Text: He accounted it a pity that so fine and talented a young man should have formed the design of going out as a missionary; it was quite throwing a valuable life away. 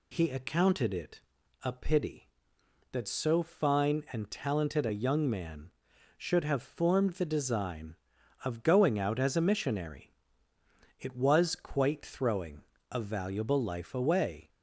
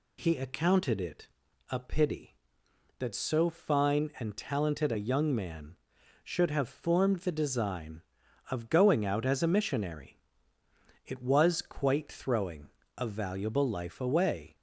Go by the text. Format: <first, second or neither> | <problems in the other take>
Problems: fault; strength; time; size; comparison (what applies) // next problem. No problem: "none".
neither | pauses between "it" and "a"; the same in both // pauses between "throwing" and "a"; slight; the same in both